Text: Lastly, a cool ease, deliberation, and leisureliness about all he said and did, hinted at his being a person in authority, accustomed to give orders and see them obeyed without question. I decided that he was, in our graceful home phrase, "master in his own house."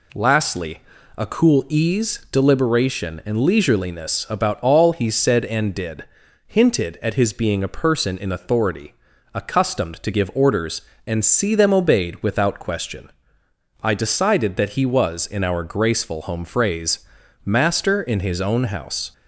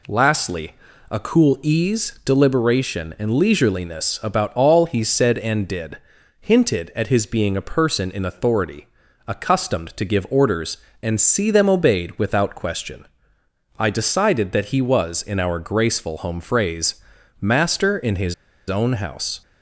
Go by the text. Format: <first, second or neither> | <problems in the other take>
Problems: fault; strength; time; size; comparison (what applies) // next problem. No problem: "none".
first | pauses between "his" and "own"; slight; at 18.3 s; 0.35 s long